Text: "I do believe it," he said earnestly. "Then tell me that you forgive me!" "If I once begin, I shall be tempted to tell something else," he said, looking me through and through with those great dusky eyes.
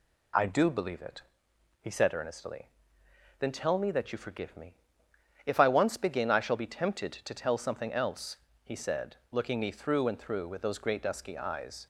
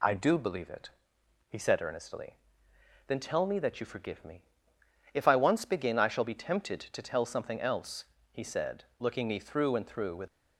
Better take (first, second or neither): first